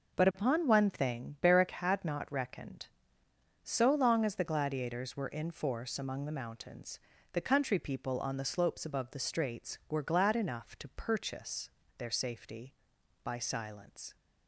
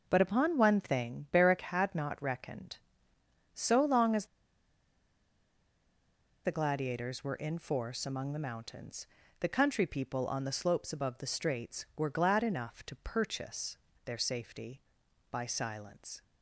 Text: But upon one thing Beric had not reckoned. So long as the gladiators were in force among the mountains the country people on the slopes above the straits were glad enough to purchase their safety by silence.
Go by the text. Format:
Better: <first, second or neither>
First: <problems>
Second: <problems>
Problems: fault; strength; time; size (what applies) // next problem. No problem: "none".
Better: first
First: pauses between "mountains" and "the"; slight; at 6.9 s; 0.32 s long // pauses between "purchase" and "their"; slight; at 11.6 s; 0.28 s long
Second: pauses between "as" and "the"; strong; at 4.2 s; 2.1 s long // pauses between "mountains" and "the"; slight; at 9.0 s; 0.32 s long // pauses between "purchase" and "their"; slight; at 13.7 s; 0.28 s long